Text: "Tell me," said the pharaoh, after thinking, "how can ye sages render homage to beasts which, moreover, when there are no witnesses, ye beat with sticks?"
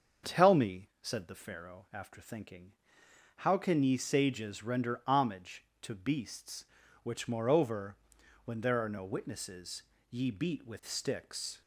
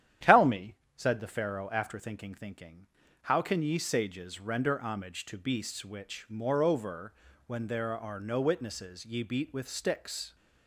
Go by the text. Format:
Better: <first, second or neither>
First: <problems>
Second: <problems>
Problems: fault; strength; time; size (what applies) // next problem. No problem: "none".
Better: first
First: starts louder than the rest; until 1.3 s; 7 dB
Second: starts louder than the rest; strong; until 1.3 s; 10.5 dB // says "thinking" twice; at 2.3 s